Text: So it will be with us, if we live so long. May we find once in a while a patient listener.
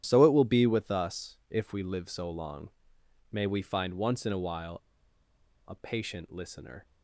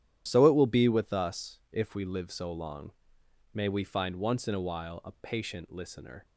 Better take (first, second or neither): second